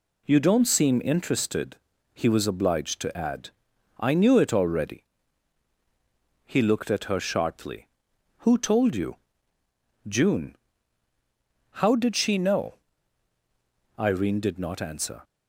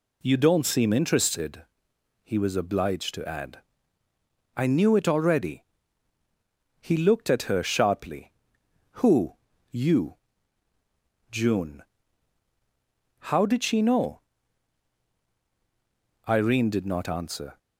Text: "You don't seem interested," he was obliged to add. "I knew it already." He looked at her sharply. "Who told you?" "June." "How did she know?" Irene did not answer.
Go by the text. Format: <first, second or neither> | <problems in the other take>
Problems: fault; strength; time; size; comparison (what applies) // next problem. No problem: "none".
first | skips "told"; at 9.5 s